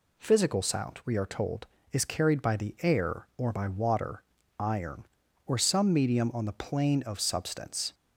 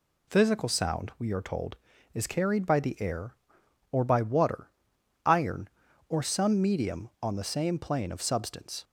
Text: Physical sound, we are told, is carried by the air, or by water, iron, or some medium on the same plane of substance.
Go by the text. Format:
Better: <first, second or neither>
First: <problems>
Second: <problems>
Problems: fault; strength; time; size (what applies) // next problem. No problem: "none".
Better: second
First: skips "same"; at 6.5 s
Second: none